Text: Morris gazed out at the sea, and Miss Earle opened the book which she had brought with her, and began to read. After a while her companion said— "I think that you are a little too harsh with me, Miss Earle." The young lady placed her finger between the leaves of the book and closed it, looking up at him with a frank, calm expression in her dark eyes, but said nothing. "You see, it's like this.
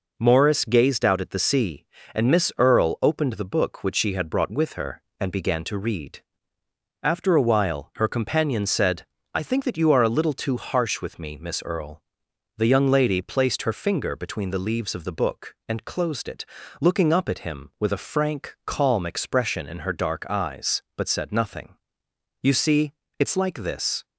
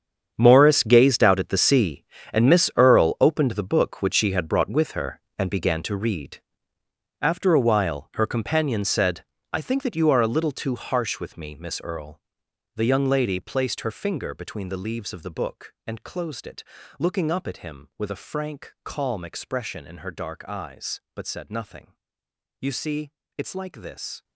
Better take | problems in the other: first | gets quieter; strong; throughout; 15.5 dB

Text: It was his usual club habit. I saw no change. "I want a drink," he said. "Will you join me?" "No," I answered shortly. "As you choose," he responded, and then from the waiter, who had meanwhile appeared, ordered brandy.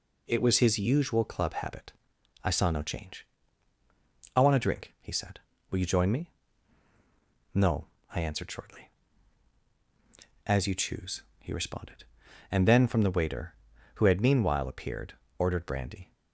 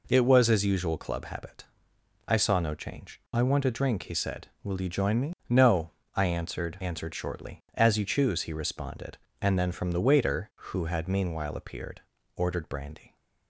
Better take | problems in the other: first | says "answered" twice; at 6.7 s

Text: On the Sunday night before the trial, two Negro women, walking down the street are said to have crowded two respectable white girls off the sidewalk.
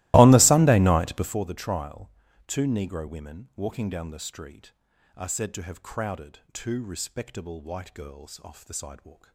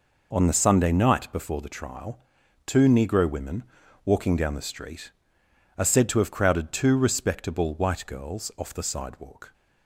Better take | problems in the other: second | starts louder than the rest; strong; until 1.4 s; 18.5 dB

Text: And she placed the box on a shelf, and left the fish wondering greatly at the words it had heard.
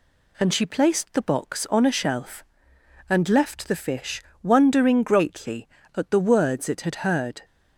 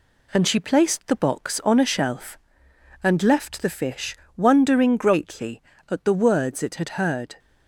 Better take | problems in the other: first | gets quieter; slight; throughout; 2.5 dB // pauses between "fish" and "wondering"; slight; at 4.1 s; 0.20 s long; slight in the first

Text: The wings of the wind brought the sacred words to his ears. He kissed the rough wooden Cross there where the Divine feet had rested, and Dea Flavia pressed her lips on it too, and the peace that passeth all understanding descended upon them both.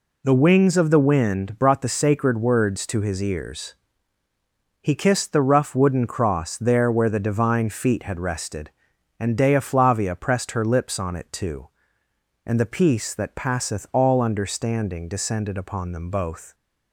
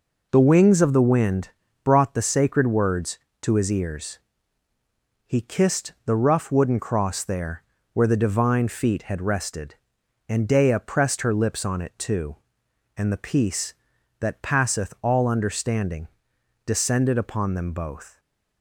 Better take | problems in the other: first | pauses between "wind" and "brought"; slight; at 1.4 s; 0.34 s long // pauses between "there" and "where"; slight; at 7.6 s; 0.30 s long // skips "Flavia"; at 10.8 s // pauses between "understanding" and "descended"; noticeable; at 16.0 s; 0.58 s long // stays silent after the last word; slight; from 18.1 s on; 0.5 s long

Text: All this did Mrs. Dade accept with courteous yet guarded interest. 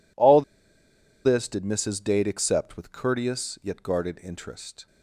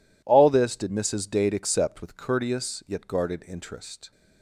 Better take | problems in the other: second | pauses between "All" and "this"; noticeable; at 0.4 s; 0.83 s long

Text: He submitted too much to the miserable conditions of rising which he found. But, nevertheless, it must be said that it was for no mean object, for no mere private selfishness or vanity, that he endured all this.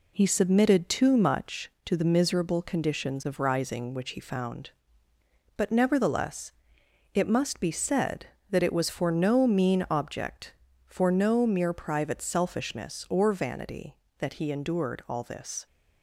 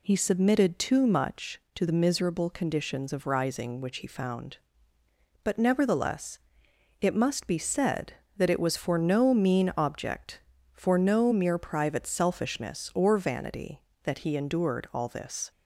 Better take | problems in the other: second | gets quieter; noticeable; throughout; 4.5 dB

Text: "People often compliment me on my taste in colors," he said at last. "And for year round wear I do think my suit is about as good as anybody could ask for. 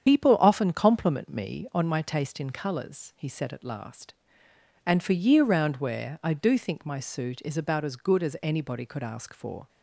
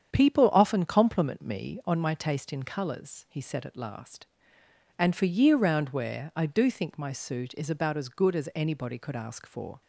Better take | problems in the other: second | loses the start of "People"; at 0.0 s; 65 ms // starts louder than the rest; strong; until 1.0 s; 8.5 dB; strong in the second

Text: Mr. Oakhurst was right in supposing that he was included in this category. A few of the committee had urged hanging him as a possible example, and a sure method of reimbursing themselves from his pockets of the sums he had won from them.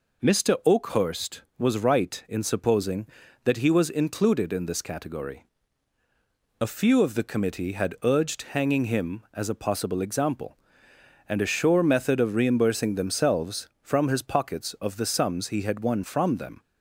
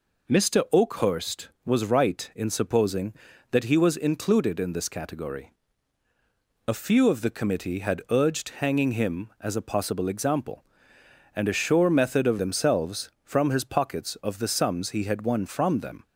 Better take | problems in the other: first | skips "reimbursing"; at 12.3 s

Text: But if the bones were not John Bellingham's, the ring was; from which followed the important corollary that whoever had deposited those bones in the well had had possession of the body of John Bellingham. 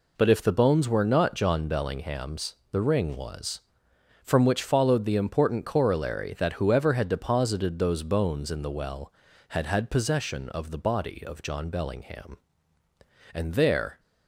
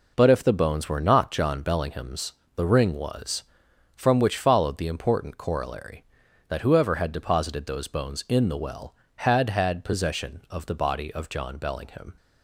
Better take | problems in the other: second | goes on to say "And there"; noticeable; from 13.3 s on; 0.66 s long

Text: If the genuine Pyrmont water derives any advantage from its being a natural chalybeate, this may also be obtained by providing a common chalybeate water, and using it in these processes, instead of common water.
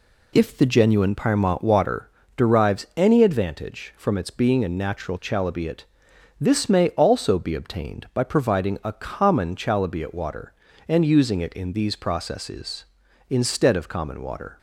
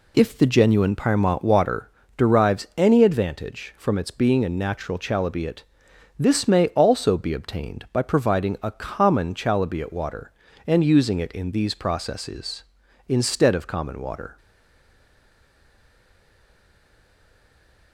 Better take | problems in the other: first | pauses between "water" and "derives"; slight; at 1.9 s; 0.26 s long; slight in the first // stays silent after the last word; strong; from 14.3 s on; 3.6 s long

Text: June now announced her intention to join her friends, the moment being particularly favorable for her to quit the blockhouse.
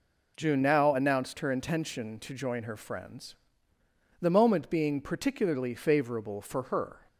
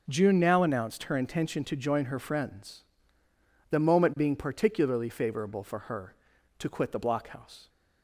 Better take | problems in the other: second | stops before "to quit the blockhouse"; at 7.0 s

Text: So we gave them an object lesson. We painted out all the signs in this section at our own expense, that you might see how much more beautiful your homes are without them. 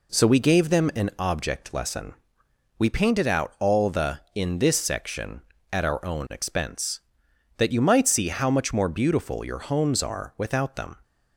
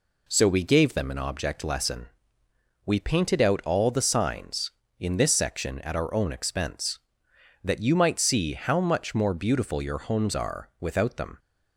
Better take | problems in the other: second | skips "signs"; at 4.2 s

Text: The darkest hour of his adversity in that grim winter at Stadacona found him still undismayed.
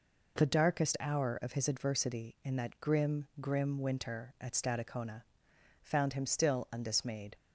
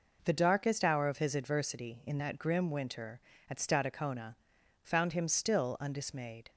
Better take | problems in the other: second | says "grim" twice; at 3.3 s // pauses between "Stadacona" and "found"; noticeable; at 5.2 s; 0.60 s long; noticeable in the second

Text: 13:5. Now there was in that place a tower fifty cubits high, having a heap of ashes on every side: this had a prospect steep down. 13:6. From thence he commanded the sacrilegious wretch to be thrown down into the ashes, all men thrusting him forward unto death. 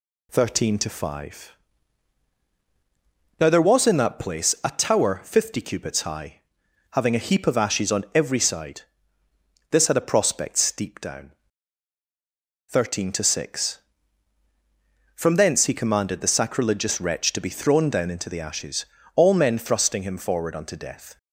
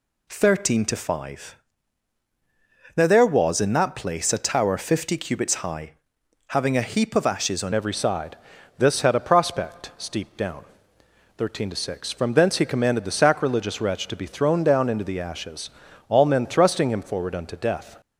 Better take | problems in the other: first | changes voice at "every"; from 7.7 s on; 10.3 s long

